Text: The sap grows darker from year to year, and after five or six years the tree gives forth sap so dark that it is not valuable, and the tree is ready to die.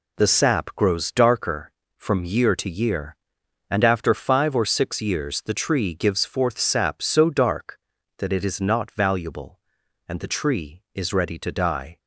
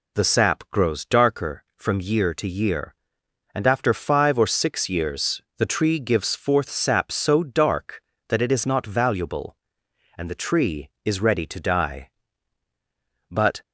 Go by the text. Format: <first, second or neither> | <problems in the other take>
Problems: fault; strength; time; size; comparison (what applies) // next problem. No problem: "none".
first | pauses between "years" and "the"; slight; at 5.4 s; 0.16 s long // goes on to say "But"; slight; from 13.2 s on; 0.32 s long